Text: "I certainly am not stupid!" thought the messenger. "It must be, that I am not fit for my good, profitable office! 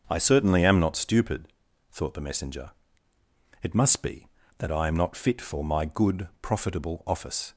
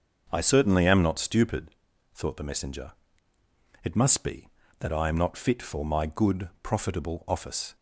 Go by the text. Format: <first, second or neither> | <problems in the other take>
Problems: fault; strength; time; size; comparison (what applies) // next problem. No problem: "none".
neither | starts louder than the rest; the same in both